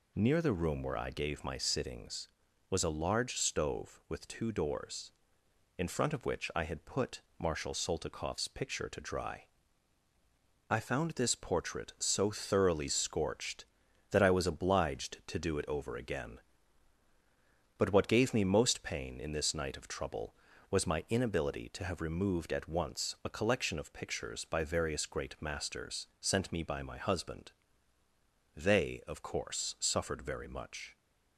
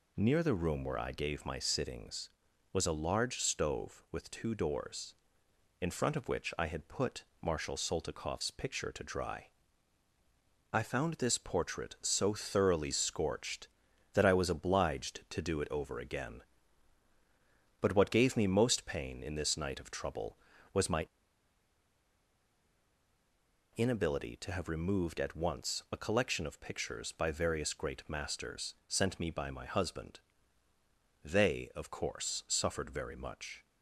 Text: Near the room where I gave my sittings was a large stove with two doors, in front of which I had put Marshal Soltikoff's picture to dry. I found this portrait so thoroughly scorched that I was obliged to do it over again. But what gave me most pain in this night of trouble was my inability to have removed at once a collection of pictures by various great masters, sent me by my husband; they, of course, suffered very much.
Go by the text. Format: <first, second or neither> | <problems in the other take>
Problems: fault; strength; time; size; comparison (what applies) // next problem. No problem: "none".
first | pauses between "put" and "Marshal"; slight; at 7.2 s; 0.16 s long; slight in the first // pauses between "my" and "inability"; strong; at 21.0 s; 2.6 s long